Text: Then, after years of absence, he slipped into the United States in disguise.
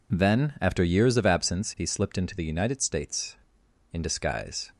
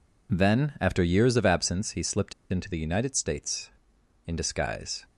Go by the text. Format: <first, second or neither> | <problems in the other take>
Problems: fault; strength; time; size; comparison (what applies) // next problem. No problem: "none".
first | pauses between "slipped" and "into"; slight; at 2.3 s; 0.18 s long